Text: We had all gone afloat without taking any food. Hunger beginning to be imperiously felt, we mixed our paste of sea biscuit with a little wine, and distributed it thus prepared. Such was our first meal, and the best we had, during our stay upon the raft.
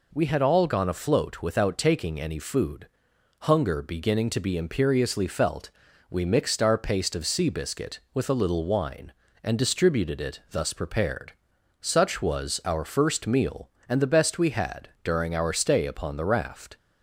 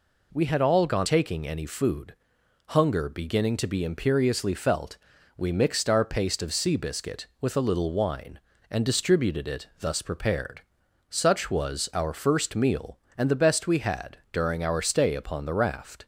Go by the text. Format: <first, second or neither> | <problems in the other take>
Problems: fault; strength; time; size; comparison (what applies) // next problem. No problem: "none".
first | skips "afloat without"; at 1.0 s